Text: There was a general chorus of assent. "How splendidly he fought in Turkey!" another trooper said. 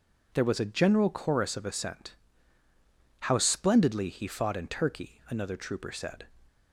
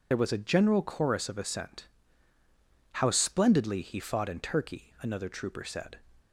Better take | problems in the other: first | loses the start of "There"; at 0.1 s; 45 ms

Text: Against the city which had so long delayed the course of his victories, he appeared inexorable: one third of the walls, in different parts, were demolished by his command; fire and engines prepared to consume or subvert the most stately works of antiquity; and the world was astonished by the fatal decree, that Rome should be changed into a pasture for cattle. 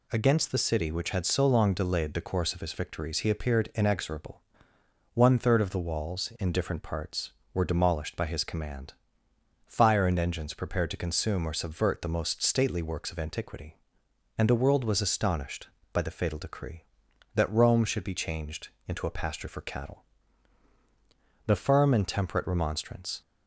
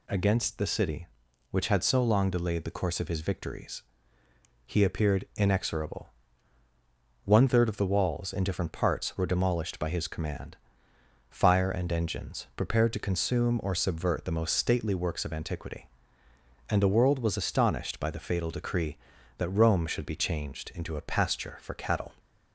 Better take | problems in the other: second | pauses between "changed" and "into"; slight; at 18.6 s; 0.18 s long // goes on to say "The firm and temperate remonstrance"; strong; from 21.4 s on; 1.7 s long

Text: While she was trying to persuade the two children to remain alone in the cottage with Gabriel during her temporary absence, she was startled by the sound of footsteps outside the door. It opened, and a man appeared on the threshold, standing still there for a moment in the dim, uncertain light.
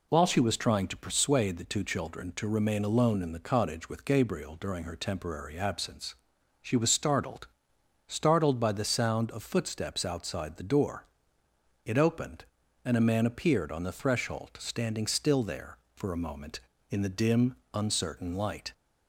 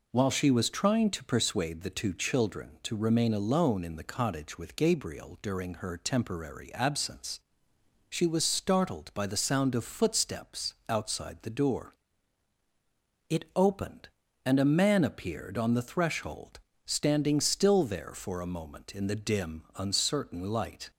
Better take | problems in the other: second | says "startled" twice; at 8.1 s

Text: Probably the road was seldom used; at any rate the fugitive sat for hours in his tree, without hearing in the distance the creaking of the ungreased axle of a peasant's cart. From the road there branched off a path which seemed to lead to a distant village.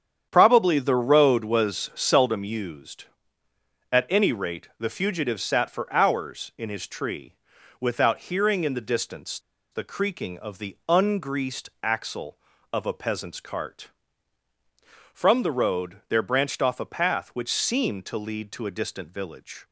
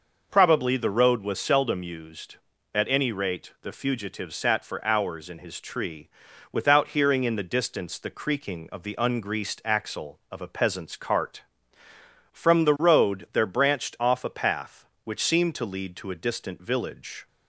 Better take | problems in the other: second | starts louder than the rest; strong; until 1.3 s; 8.5 dB // pauses between "distance" and "the"; slight; at 9.3 s; 0.33 s long

